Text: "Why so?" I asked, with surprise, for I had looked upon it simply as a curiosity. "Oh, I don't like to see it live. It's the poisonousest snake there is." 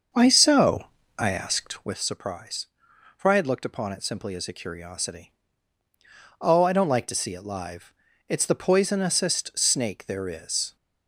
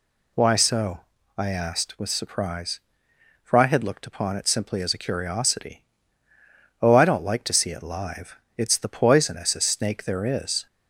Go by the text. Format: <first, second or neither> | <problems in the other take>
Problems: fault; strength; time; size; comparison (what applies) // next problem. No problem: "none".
second | starts louder than the rest; until 2.0 s; 6.5 dB